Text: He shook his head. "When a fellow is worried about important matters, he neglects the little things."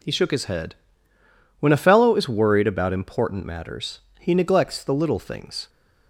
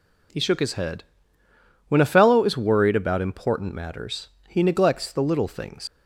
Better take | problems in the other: first | leaves "things" unfinished; at 5.8 s; 100 ms

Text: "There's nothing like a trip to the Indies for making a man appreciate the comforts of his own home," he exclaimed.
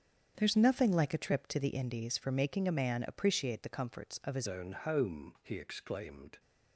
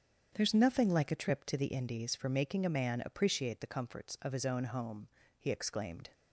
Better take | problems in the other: second | starts louder than the rest; strong; until 1.3 s; 8 dB; strong in the second // changes voice at "own"; from 4.4 s on; 1.9 s long

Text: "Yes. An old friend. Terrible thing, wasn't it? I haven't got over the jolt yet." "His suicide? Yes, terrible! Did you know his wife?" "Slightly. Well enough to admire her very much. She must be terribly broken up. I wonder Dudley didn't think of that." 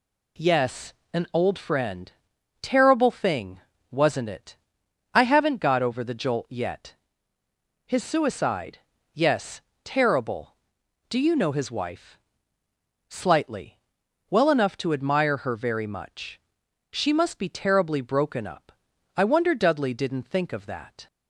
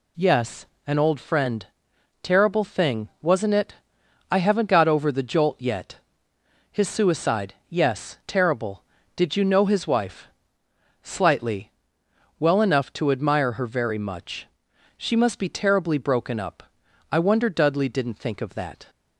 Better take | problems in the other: second | says "Do" for "Did"; at 11.0 s

